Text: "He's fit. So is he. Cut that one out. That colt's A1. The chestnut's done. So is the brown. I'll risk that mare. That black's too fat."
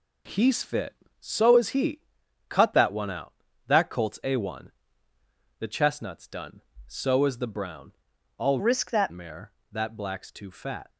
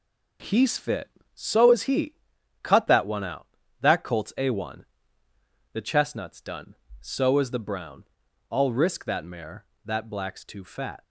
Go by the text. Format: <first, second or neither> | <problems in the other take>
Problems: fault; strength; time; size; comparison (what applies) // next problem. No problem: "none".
second | changes voice from "risk" to "that"; from 8.5 to 9.1 s; 0.6 s long